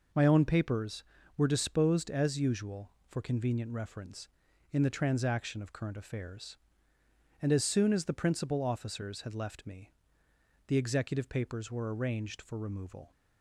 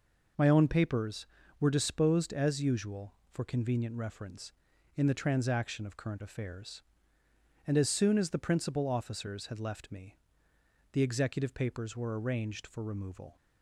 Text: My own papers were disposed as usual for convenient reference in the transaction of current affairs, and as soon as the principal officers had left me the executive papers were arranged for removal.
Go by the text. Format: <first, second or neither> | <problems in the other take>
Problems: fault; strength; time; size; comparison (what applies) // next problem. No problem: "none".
neither | pauses between "me" and "the"; noticeable; the same in both